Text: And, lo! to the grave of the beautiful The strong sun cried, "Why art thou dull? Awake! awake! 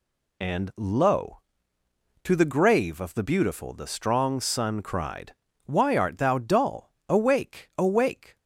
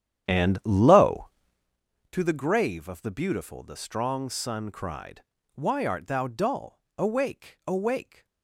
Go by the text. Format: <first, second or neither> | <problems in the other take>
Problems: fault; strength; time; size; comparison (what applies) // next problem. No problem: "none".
first | starts louder than the rest; strong; until 1.8 s; 10 dB